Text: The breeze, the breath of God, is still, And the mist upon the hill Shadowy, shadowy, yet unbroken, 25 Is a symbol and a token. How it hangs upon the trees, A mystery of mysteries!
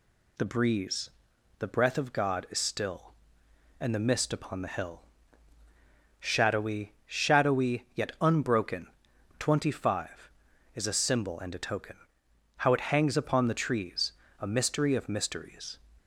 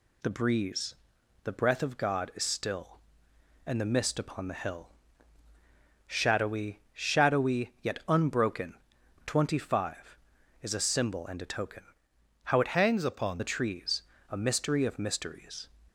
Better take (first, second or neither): first